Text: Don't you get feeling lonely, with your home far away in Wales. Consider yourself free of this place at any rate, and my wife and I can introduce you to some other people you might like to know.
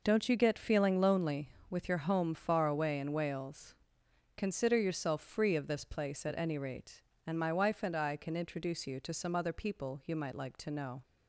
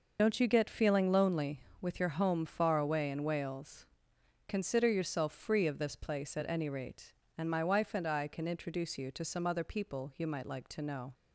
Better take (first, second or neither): first